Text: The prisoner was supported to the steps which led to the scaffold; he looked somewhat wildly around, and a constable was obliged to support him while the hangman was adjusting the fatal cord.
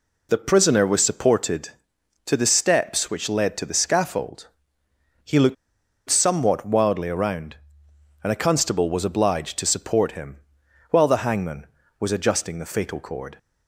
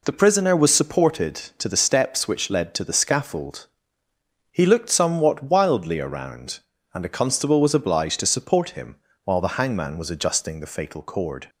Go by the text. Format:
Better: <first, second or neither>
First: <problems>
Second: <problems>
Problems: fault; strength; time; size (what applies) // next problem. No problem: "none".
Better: second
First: pauses between "looked" and "somewhat"; noticeable; at 5.5 s; 0.54 s long // pauses between "him" and "while"; noticeable; at 10.3 s; 0.52 s long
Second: pauses between "him" and "while"; slight; at 8.9 s; 0.26 s long